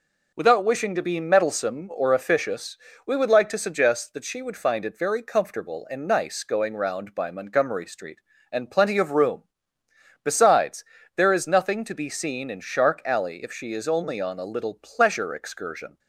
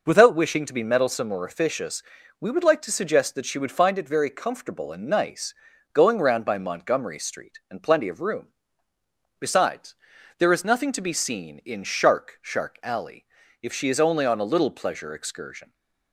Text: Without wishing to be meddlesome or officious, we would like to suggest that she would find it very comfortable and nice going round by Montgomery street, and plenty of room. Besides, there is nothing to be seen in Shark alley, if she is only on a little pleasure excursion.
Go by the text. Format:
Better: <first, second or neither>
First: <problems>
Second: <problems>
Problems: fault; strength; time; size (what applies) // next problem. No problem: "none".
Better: first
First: none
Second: pauses between "nice" and "going"; at 5.5 s; 0.40 s long // says "Shark" twice; at 12.4 s